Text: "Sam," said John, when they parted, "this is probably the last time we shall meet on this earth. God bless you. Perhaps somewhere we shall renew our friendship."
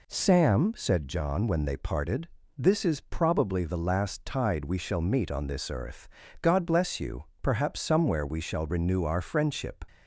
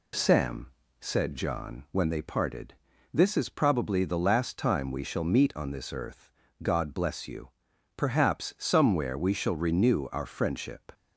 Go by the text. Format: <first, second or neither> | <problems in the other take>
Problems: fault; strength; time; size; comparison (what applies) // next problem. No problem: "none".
second | says "tide" for "time"; at 4.2 s